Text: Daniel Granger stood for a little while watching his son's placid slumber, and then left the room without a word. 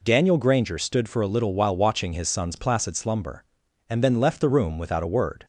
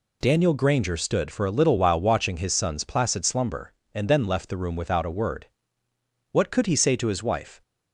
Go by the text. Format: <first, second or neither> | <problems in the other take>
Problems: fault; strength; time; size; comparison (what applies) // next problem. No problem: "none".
first | goes on to say "What could he say to his wife"; noticeable; from 6.3 s on; 1.2 s long